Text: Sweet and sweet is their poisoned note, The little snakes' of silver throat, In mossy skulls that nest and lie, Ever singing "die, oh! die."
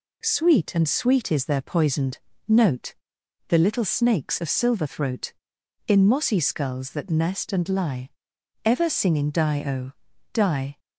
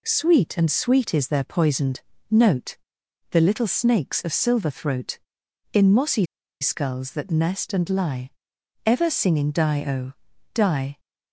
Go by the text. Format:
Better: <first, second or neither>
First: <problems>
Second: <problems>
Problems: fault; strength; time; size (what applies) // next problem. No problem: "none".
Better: first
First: pauses between "poisoned" and "note"; slight; at 2.1 s; 0.28 s long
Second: pauses between "poisoned" and "note"; slight; at 2.0 s; 0.28 s long // pauses between "mossy" and "skulls"; slight; at 6.2 s; 0.35 s long